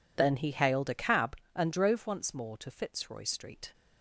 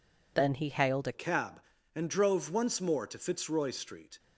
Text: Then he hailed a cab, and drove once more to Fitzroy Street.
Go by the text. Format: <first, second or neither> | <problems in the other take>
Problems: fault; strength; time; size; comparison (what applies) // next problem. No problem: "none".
first | changes voice at "cab"; from 1.1 s on; 3.0 s long